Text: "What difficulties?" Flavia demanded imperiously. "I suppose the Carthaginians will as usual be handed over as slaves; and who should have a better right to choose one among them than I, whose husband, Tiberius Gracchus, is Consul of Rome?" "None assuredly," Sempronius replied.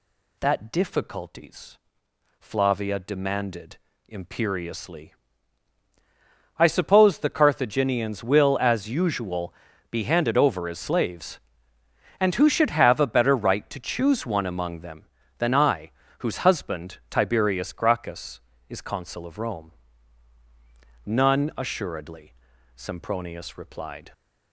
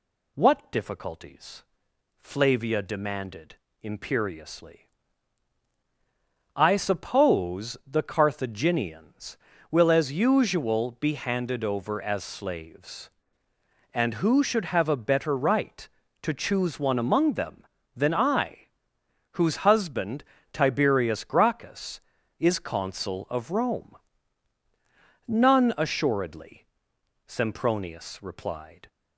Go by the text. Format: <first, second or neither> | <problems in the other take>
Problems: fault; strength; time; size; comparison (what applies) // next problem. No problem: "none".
second | says "That" for "What"; at 0.3 s // pauses between "demanded" and "imperiously"; slight; at 3.7 s; 0.30 s long; slight in the second // pauses between "usual" and "be"; slight; at 9.5 s; 0.36 s long